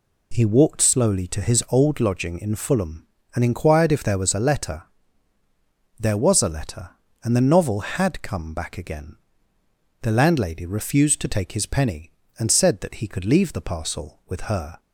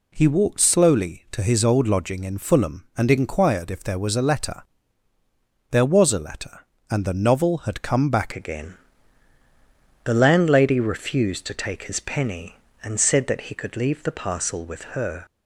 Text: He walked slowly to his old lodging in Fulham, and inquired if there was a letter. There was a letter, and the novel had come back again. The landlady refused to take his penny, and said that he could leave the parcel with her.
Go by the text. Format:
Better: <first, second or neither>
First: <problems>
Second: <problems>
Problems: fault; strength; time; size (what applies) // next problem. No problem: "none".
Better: first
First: none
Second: changes voice at "again"; from 8.3 s on; 6.9 s long